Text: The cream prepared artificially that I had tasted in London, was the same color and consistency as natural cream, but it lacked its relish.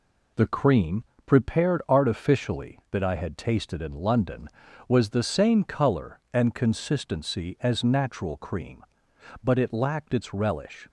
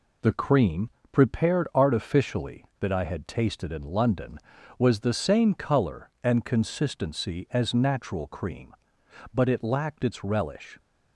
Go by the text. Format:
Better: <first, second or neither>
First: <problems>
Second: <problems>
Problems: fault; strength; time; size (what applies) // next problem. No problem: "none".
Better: neither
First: pauses between "cream" and "prepared"; slight; at 1.0 s; 0.22 s long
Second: pauses between "cream" and "prepared"; slight; at 0.8 s; 0.22 s long